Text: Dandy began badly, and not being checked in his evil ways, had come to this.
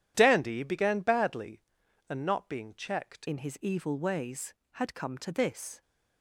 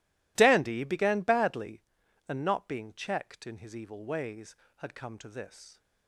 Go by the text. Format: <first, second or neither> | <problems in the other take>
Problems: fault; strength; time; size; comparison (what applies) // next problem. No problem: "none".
second | changes voice at "in"; from 3.2 s on; 2.6 s long